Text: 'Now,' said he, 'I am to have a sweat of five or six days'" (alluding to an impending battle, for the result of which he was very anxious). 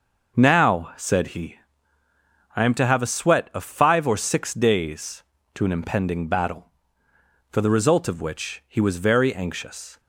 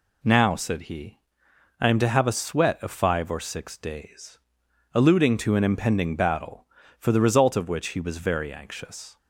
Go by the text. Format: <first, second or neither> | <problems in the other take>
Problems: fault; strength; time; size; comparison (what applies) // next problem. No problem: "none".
second | skips "alluding"; at 5.3 s